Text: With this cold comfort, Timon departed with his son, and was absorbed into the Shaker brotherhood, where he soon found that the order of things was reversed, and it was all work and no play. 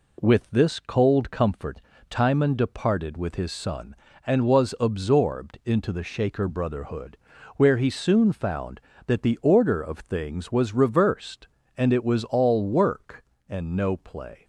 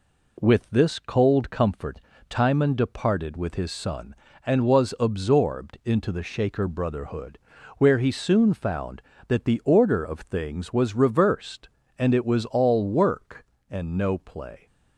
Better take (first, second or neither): neither